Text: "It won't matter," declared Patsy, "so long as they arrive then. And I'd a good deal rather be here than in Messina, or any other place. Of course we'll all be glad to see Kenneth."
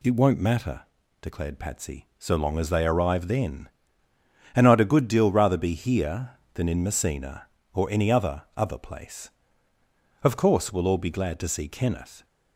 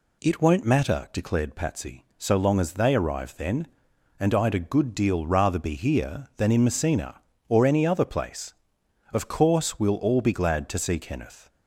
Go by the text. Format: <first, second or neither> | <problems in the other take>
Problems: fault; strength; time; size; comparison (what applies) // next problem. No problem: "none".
second | says "other" twice; at 8.5 s